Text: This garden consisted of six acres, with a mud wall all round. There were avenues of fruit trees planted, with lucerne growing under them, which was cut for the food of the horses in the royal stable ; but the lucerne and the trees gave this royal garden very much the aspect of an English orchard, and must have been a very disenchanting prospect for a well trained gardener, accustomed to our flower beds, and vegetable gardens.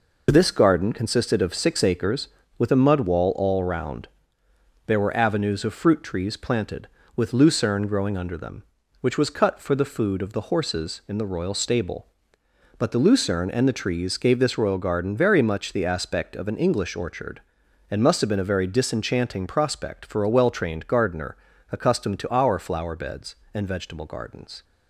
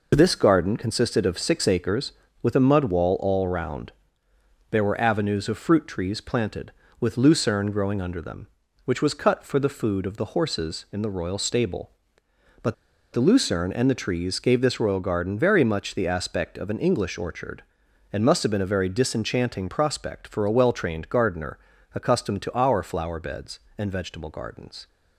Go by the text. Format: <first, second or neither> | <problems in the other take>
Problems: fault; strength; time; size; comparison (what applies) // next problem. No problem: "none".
first | pauses between "but" and "the"; at 12.7 s; 0.38 s long